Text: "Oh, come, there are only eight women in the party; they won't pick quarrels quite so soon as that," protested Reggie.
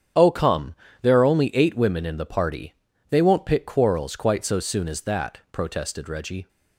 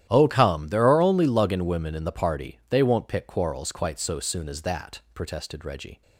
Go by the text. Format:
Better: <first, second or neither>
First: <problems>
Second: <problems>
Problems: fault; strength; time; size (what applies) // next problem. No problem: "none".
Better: first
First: starts louder than the rest; strong; until 1.4 s; 8.5 dB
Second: starts louder than the rest; strong; until 1.1 s; 12 dB // says "luggin" for "eight"; at 1.2 s